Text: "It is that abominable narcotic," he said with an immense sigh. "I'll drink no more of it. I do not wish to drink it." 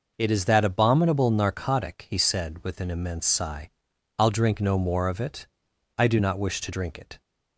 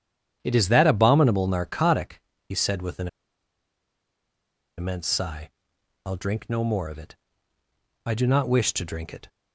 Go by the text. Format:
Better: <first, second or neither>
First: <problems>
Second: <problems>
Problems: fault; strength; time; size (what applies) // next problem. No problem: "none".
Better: first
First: none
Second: starts louder than the rest; strong; until 1.4 s; 9.5 dB // pauses between "an" and "immense"; strong; at 3.0 s; 1.6 s long